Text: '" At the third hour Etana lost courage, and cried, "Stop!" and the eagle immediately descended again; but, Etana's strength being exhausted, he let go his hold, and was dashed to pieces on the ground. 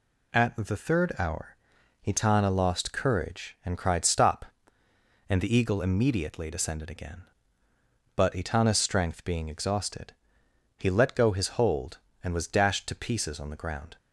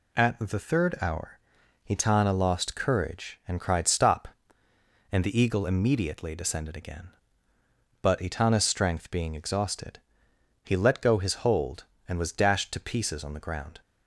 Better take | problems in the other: neither | pauses between "hour" and "Etana"; noticeable; the same in both

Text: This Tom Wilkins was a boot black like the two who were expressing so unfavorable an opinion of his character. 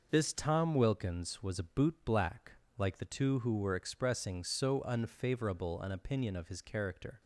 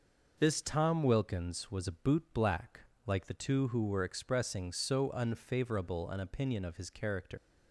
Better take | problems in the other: first | pauses between "black" and "like"; slight; at 2.8 s; 0.22 s long; slight in the first // leaves "character" unfinished; at 7.3 s; 110 ms

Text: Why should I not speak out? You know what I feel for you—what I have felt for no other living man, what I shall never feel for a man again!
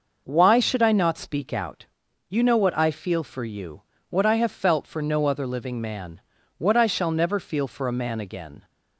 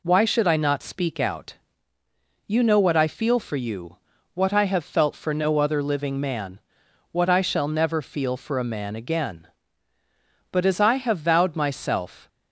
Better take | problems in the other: first | goes on to say "But as I have vowed myself"; strong; from 10.4 s on; 1.7 s long

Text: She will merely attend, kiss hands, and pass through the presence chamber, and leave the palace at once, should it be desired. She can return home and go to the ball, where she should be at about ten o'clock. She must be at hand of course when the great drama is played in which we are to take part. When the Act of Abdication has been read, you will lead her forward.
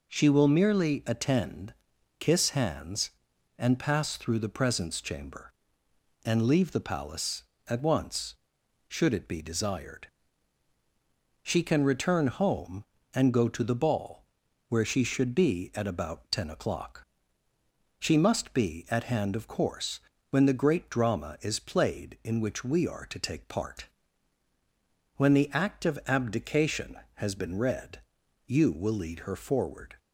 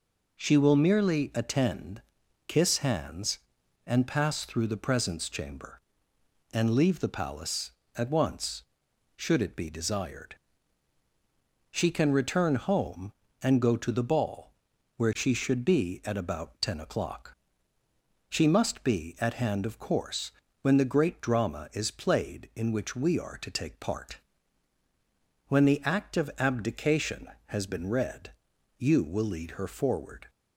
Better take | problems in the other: neither | pauses between "course" and "when"; slight; the same in both

